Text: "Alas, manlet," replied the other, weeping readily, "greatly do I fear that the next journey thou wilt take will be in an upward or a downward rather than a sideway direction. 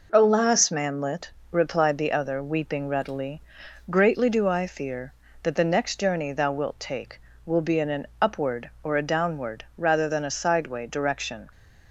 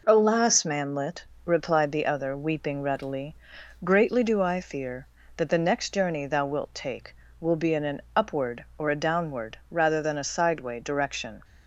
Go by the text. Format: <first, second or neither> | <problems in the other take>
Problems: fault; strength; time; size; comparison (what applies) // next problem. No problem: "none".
neither | none